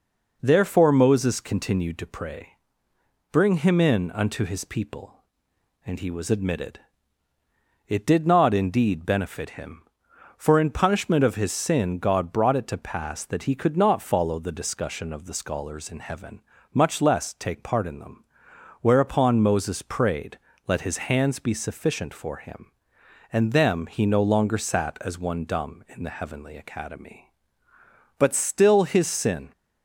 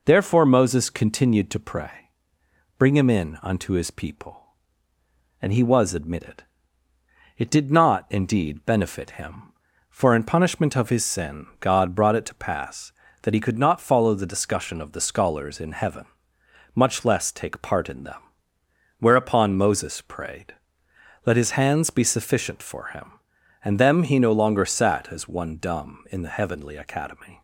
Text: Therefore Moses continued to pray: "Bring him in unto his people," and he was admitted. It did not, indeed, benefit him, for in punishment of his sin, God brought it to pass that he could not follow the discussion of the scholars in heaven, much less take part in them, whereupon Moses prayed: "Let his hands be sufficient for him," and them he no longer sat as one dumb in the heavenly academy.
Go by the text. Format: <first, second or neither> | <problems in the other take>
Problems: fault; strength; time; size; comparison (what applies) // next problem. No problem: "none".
second | goes on to say "But still his sin"; from 28.1 s on; 1.3 s long